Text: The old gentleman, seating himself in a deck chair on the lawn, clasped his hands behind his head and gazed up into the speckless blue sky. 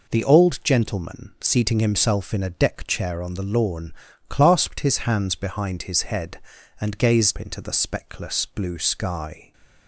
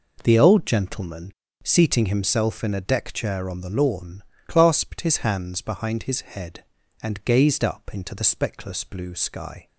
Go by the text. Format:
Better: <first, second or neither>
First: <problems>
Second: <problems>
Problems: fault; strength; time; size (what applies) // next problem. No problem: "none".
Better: second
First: skips "up"; at 7.3 s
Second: none